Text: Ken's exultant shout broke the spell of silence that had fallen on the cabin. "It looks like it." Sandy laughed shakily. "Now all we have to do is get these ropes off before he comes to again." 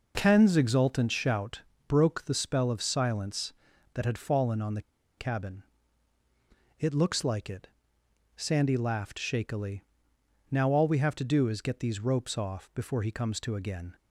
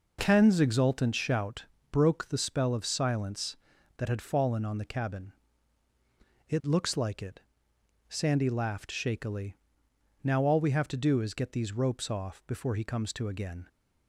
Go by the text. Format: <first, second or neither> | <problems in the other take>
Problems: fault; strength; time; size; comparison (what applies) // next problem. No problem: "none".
second | pauses between "shout" and "broke"; slight; at 1.5 s; 0.28 s long; slight in the second // pauses between "the" and "cabin"; at 4.7 s; 0.37 s long